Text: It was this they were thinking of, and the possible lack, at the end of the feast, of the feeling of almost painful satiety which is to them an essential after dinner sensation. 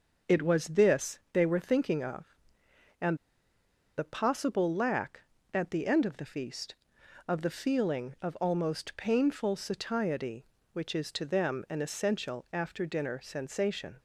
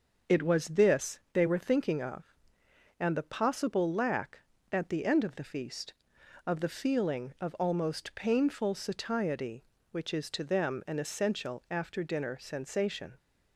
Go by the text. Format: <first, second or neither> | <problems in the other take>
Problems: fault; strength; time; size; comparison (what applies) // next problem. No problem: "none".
second | starts louder than the rest; until 1.4 s; 6.5 dB; also in the second // pauses between "and" and "the"; noticeable; at 3.1 s; 0.81 s long